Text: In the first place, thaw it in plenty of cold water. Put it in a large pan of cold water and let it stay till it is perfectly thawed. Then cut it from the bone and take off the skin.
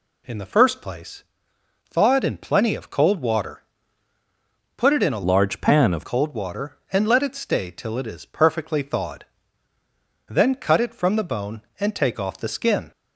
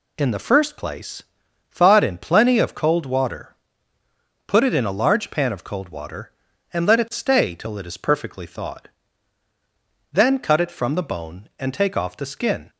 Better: second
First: changes voice from "large" to "of"; from 5.2 to 6.0 s; 0.8 s long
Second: none

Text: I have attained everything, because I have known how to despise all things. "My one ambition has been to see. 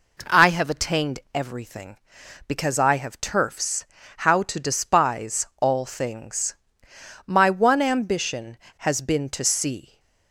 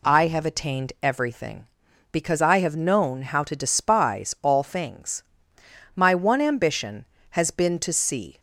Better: second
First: says "turfs" for "known"; at 3.1 s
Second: none

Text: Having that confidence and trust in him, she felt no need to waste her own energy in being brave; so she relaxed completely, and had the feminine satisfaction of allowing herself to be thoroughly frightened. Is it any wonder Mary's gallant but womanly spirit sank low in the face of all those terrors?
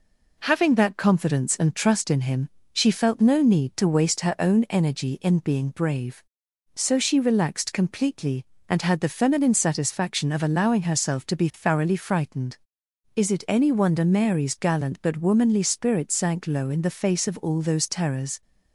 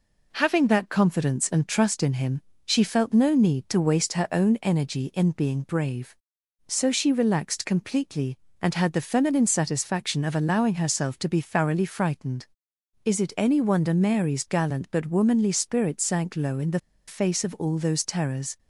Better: first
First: none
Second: pauses between "the" and "face"; slight; at 16.7 s; 0.29 s long

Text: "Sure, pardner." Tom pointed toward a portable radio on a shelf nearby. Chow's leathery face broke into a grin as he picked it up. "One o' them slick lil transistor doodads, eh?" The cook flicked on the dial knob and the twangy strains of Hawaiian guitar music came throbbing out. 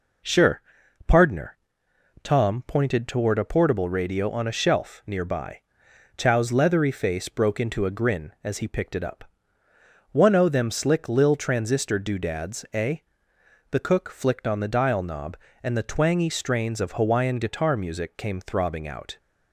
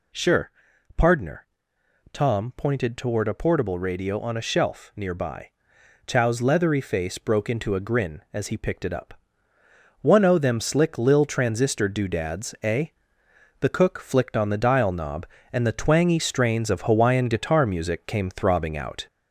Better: first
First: none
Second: gets louder; slight; throughout; 3.5 dB

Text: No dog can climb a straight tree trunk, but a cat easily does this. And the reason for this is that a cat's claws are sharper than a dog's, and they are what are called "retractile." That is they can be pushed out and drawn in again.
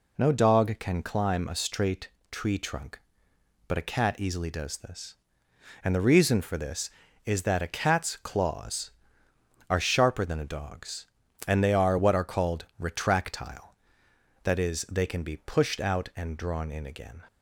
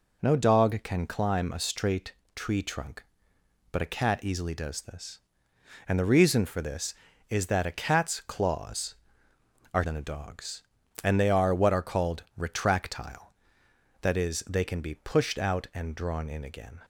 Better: first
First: pauses between "straight" and "tree"; slight; at 2.0 s; 0.22 s long // pauses between "called" and "retractile"; slight; at 12.6 s; 0.16 s long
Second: pauses between "straight" and "tree"; slight; at 2.1 s; 0.22 s long // skips "sharper"; at 9.8 s // pauses between "called" and "retractile"; slight; at 12.2 s; 0.16 s long

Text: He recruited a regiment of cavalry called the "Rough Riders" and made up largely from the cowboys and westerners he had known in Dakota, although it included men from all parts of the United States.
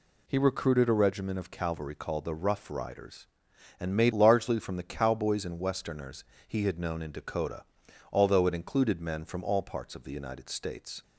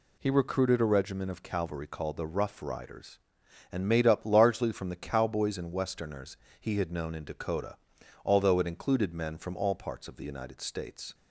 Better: second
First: skips "up"; at 4.1 s // pauses between "westerners" and "he"; slight; at 6.2 s; 0.24 s long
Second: pauses between "westerners" and "he"; slight; at 6.3 s; 0.24 s long

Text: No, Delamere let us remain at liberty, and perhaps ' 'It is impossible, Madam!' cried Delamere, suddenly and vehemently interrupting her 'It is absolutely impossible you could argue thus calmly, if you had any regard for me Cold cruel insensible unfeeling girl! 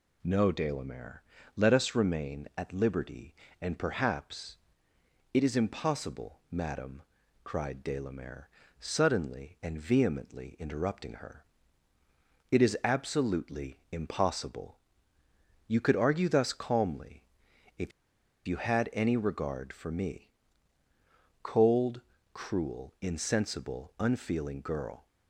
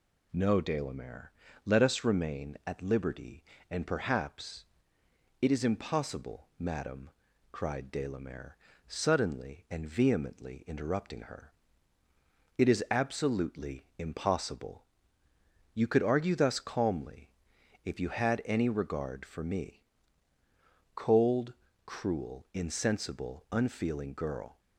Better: second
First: pauses between "Delamere" and "let"; slight; at 1.2 s; 0.34 s long // pauses between "her" and "It"; at 11.4 s; 1.0 s long // pauses between "impossible" and "you"; noticeable; at 14.7 s; 0.90 s long // pauses between "if" and "you"; noticeable; at 17.9 s; 0.57 s long // pauses between "me" and "Cold"; at 20.3 s; 1.1 s long // pauses between "Cold" and "cruel"; slight; at 22.0 s; 0.32 s long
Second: pauses between "Delamere" and "let"; slight; at 1.3 s; 0.34 s long // pauses between "her" and "It"; at 11.5 s; 1.0 s long // pauses between "impossible" and "you"; noticeable; at 14.8 s; 0.90 s long // pauses between "me" and "Cold"; at 19.8 s; 1.1 s long // pauses between "Cold" and "cruel"; slight; at 21.5 s; 0.32 s long

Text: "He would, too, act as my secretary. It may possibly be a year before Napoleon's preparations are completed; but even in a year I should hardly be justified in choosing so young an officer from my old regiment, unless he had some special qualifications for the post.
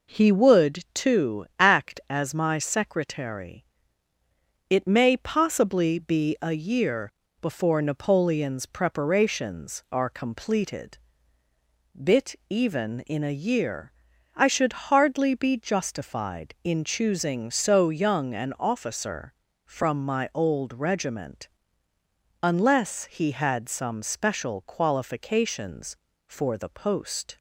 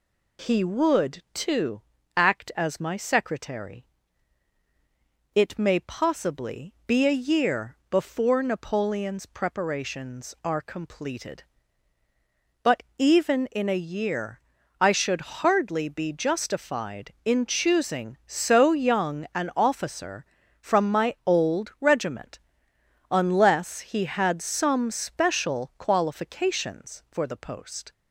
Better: second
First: pauses between "year" and "before"; slight; at 7.1 s; 0.30 s long // says "bit" for "but"; at 11.9 s // pauses between "year" and "I"; at 13.9 s; 0.44 s long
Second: pauses between "year" and "I"; at 14.4 s; 0.40 s long

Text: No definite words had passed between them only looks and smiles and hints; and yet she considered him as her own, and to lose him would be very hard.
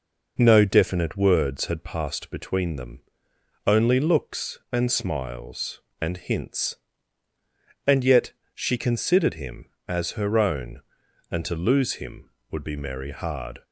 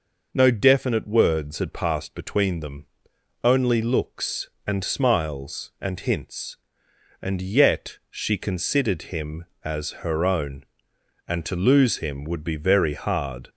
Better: second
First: pauses between "them" and "only"; noticeable; at 2.9 s; 0.66 s long // pauses between "yet" and "she"; slight; at 8.3 s; 0.20 s long // says "merry" for "very"; at 12.7 s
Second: pauses between "them" and "only"; noticeable; at 2.8 s; 0.56 s long

